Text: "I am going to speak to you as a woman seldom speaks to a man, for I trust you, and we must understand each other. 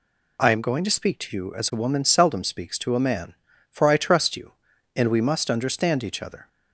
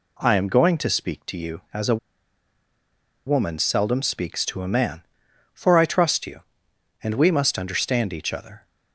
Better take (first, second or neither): first